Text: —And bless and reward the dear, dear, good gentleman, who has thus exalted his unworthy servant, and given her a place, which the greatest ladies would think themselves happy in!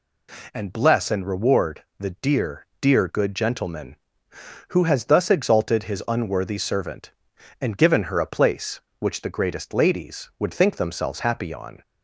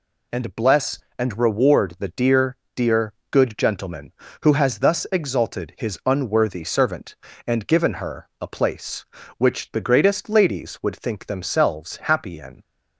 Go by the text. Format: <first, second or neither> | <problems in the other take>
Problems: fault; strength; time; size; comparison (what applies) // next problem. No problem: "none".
second | pauses between "reward" and "the"; slight; at 1.8 s; 0.16 s long // says "on" for "in"; at 11.5 s